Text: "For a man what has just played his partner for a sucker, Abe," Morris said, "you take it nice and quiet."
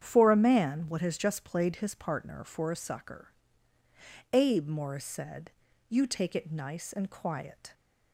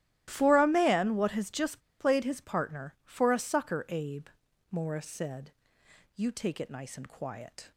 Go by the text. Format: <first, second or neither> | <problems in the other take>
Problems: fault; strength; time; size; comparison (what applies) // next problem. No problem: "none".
first | starts louder than the rest; strong; until 1.2 s; 13.5 dB; strong in the first // pauses between "just" and "played"; slight; at 1.8 s; 0.18 s long